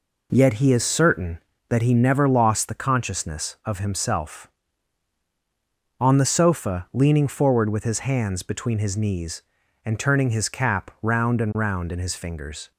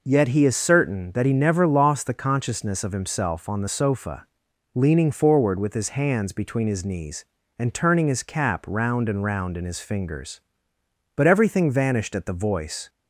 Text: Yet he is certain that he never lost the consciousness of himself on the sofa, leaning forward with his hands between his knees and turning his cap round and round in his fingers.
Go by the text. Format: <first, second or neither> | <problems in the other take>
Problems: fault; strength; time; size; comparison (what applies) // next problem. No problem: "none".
first | goes on to say "But everything vanished at the voice"; strong; from 11.1 s on; 1.7 s long